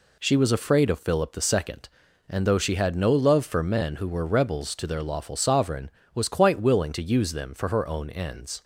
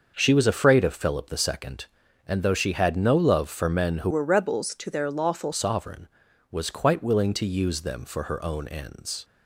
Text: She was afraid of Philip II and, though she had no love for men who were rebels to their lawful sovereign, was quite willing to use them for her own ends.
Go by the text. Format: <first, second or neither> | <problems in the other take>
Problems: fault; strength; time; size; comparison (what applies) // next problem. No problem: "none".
first | starts louder than the rest; noticeable; until 1.1 s; 6 dB // changes voice from "were" to "lawful"; from 4.1 to 5.5 s; 1.4 s long